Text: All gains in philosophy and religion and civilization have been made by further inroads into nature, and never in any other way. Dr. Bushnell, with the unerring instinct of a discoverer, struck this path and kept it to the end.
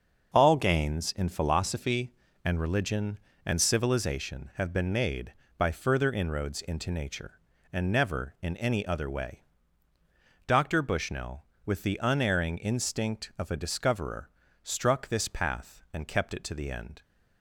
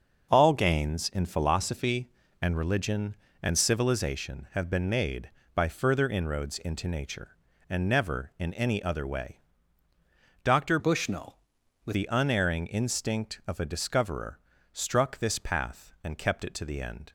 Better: first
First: starts louder than the rest; until 1.3 s; 6 dB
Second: starts louder than the rest; until 1.3 s; 6 dB // changes voice from "Bushnell" to "with"; from 10.7 to 11.9 s; 1.2 s long

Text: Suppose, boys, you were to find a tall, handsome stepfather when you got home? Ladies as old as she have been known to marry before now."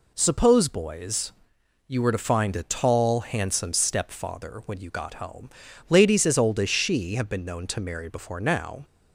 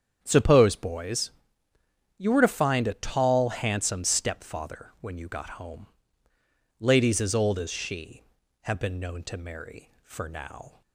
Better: first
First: none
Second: starts louder than the rest; strong; until 1.2 s; 8.5 dB // says "for" for "before"; at 10.0 s

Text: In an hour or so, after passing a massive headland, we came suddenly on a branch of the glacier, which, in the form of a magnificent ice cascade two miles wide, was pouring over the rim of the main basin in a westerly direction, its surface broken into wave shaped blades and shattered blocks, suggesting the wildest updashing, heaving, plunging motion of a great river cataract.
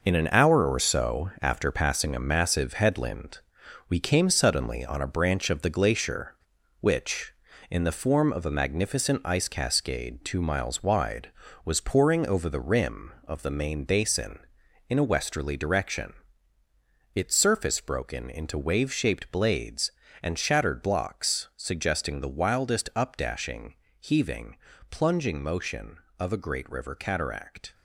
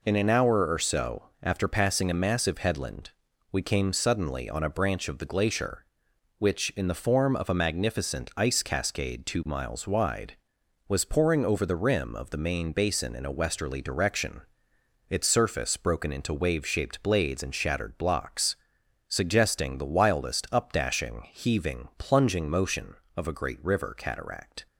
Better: second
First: gets quieter; strong; throughout; 8.5 dB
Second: none

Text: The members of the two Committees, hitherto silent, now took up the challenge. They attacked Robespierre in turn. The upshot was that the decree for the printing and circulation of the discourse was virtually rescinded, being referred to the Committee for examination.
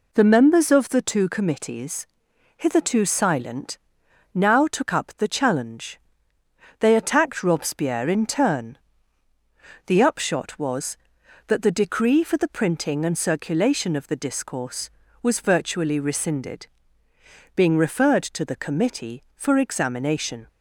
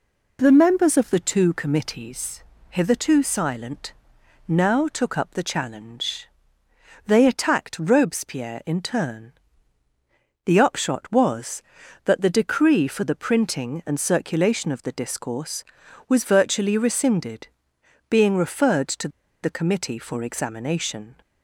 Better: first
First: none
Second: pauses between "to" and "the"; slight; at 19.0 s; 0.34 s long

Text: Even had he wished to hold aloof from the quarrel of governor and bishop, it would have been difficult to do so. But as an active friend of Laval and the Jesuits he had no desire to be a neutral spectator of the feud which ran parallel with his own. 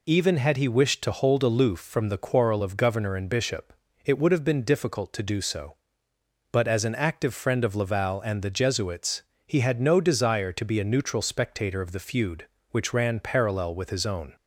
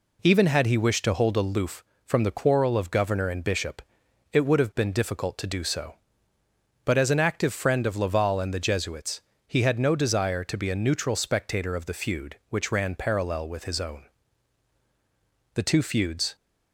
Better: first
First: pauses between "Jesuits" and "he"; slight; at 9.2 s; 0.22 s long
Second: pauses between "Jesuits" and "he"; slight; at 9.2 s; 0.24 s long // goes on to say "The two feuds"; noticeable; from 15.5 s on; 0.82 s long

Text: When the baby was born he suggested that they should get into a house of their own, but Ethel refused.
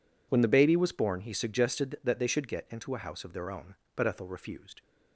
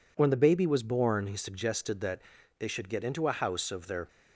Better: first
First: none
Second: pauses between "that" and "they"; at 2.2 s; 0.38 s long // stops before "own but Ethel refused"; at 4.0 s

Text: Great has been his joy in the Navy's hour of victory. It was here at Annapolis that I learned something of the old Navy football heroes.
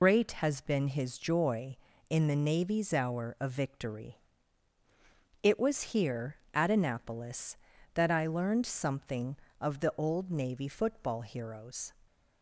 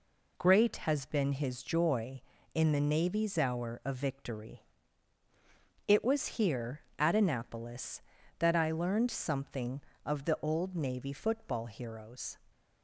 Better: second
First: loses the start of "Great"; at 0.0 s; 90 ms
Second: none

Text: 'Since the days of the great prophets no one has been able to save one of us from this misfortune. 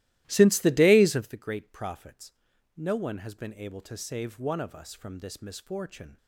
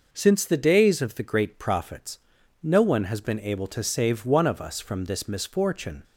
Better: second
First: starts louder than the rest; strong; until 1.4 s; 16 dB // pauses between "prophets" and "no"; at 2.3 s; 0.44 s long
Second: pauses between "prophets" and "no"; at 2.1 s; 0.44 s long

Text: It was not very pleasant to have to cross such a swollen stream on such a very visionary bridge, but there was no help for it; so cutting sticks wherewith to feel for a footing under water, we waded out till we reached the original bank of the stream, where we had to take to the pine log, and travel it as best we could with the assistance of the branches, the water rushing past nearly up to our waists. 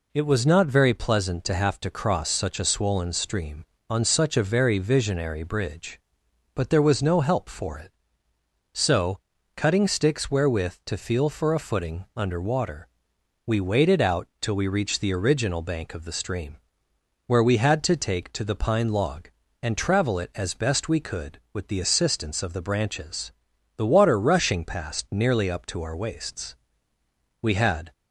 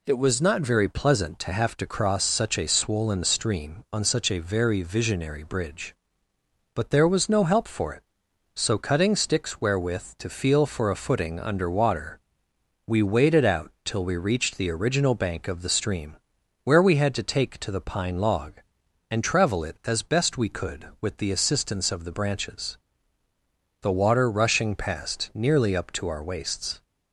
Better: second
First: pauses between "so" and "cutting"; slight; at 9.1 s; 0.34 s long // pauses between "out" and "till"; slight; at 14.2 s; 0.16 s long // goes on to say "We had"; from 27.4 s on; 0.50 s long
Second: none

